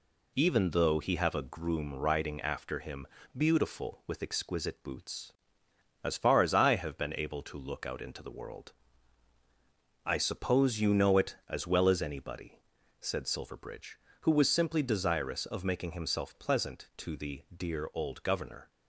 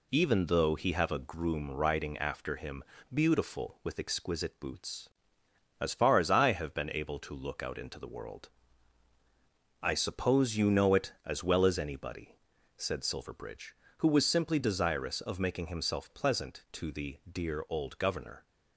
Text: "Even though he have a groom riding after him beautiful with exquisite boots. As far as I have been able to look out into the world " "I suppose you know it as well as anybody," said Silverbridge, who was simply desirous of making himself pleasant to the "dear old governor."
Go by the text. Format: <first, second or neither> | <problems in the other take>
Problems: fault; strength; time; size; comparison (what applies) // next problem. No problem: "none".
neither | pauses between "him" and "beautiful"; slight; the same in both